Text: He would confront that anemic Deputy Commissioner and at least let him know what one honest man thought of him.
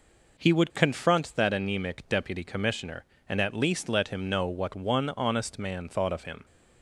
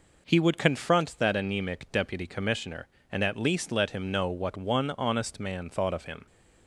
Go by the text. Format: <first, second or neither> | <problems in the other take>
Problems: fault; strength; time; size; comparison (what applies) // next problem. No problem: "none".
neither | none